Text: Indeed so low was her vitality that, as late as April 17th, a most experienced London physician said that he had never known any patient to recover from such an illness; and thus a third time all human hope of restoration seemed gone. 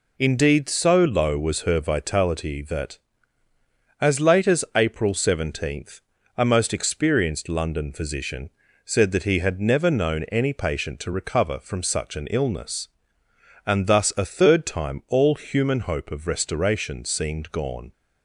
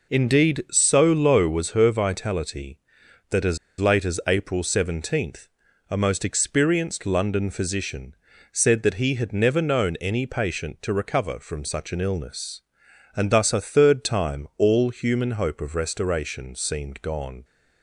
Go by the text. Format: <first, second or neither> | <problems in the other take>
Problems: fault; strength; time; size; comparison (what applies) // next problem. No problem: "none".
first | pauses between "as" and "late"; slight; at 3.5 s; 0.22 s long // pauses between "physician" and "said"; slight; at 8.1 s; 0.36 s long; slight in the first